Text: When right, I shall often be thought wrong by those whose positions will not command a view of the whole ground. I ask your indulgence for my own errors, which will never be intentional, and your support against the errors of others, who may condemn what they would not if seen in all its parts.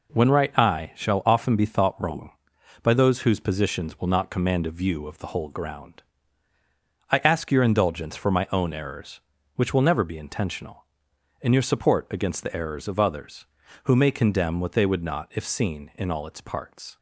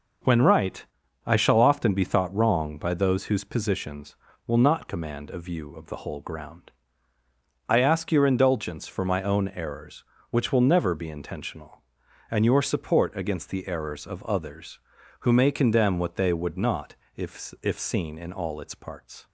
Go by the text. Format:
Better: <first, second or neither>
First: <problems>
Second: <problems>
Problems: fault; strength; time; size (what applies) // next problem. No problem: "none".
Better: first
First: none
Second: pauses between "not" and "if"; slight; at 16.9 s; 0.22 s long // says "if" twice; at 17.6 s